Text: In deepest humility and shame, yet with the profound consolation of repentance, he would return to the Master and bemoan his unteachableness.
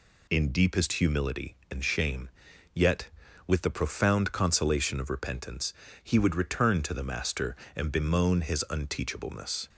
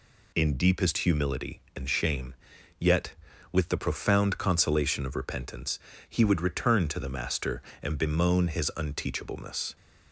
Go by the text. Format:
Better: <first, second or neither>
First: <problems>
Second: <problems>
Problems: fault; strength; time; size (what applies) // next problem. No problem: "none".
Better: neither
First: none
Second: none